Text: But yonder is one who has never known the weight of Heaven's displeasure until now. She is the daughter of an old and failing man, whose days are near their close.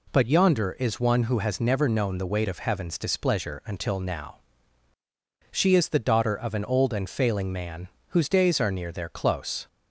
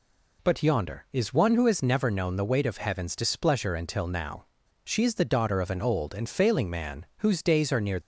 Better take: first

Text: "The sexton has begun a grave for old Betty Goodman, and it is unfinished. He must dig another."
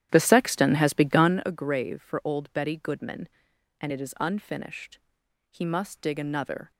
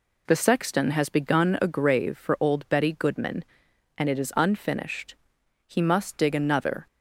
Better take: second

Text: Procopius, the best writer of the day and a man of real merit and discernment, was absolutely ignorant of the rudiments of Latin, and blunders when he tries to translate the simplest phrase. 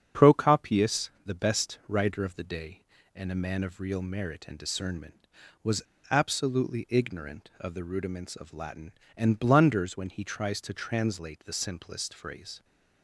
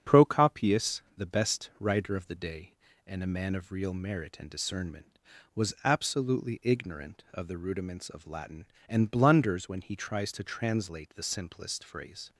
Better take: second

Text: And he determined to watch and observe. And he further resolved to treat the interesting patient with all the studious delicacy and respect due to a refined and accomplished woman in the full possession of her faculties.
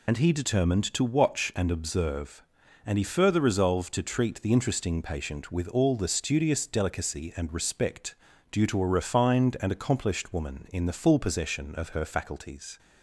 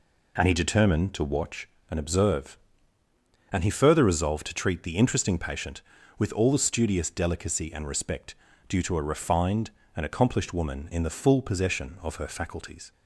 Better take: second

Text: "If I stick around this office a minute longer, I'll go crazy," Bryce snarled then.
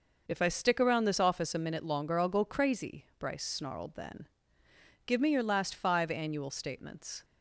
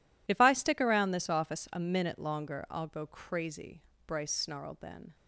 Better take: second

